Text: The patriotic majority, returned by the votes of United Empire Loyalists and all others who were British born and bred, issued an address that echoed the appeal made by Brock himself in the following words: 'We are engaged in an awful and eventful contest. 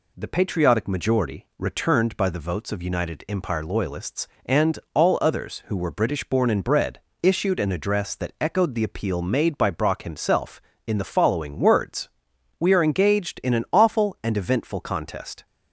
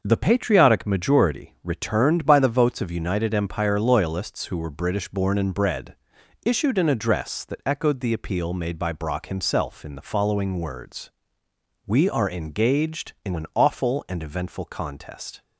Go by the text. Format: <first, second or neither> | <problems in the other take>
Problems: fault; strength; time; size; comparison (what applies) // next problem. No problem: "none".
first | starts louder than the rest; until 1.0 s; 6 dB // skips "and all others"; at 4.4 s